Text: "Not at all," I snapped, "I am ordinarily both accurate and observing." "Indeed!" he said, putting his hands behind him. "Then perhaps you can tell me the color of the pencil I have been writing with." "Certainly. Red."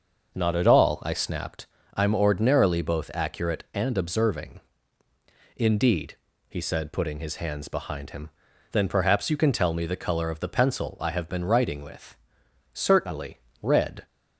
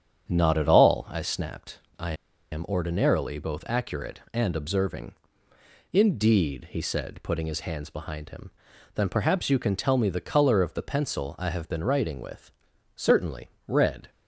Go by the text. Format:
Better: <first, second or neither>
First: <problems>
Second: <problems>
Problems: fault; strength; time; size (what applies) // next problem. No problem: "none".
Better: first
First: starts louder than the rest; noticeable; until 1.3 s; 6 dB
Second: starts louder than the rest; strong; until 1.3 s; 8 dB // pauses between "I" and "am"; at 2.1 s; 0.41 s long